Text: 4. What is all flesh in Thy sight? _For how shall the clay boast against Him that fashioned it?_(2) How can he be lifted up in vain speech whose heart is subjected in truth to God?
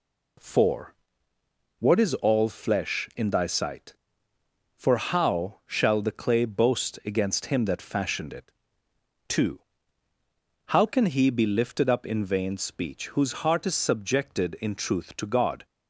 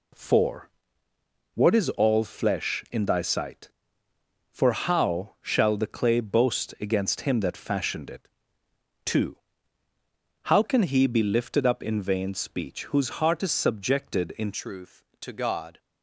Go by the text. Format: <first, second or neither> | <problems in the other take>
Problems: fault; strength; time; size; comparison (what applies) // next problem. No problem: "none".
first | changes voice at "truth"; from 14.5 s on; 1.2 s long